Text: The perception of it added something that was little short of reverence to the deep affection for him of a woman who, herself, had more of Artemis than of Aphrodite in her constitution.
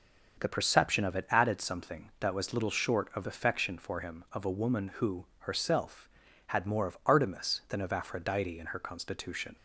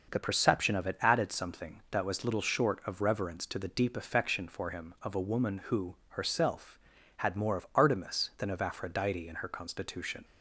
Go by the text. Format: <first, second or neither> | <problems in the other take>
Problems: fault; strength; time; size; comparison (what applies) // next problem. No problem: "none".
second | starts louder than the rest; until 1.4 s; 6.5 dB // skips "reverence to the deep"; at 3.2 s